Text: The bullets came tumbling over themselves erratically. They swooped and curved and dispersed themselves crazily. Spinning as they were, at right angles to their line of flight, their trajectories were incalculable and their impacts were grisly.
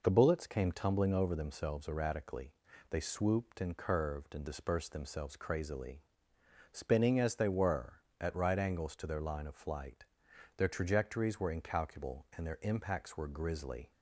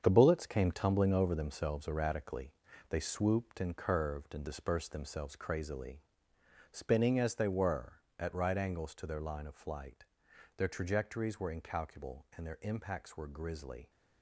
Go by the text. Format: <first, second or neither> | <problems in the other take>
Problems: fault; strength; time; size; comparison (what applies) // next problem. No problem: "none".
first | gets quieter; strong; throughout; 8.5 dB